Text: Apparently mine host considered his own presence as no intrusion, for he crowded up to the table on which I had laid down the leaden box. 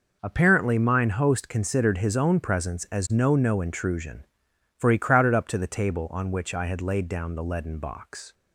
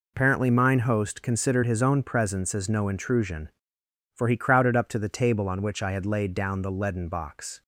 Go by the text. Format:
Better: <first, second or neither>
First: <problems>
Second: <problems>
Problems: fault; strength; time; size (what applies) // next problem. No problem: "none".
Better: second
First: says "no" twice; at 3.3 s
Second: none